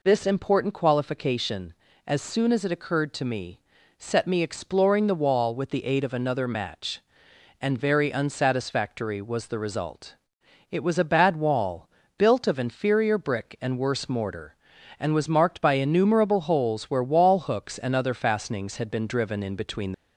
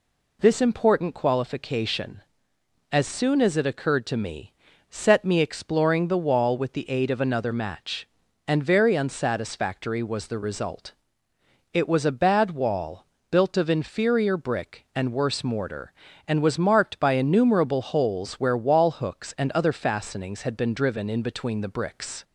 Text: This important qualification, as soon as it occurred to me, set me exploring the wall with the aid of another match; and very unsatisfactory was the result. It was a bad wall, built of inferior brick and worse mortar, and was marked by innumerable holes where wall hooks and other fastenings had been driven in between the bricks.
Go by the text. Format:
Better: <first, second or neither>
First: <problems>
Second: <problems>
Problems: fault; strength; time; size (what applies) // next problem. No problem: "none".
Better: second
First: stops before "the bricks"; at 19.9 s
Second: none